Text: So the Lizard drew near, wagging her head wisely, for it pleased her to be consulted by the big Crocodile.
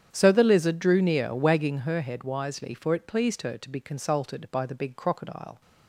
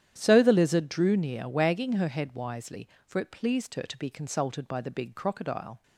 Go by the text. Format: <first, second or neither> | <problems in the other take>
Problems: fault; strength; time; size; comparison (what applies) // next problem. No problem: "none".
neither | starts louder than the rest; strong; the same in both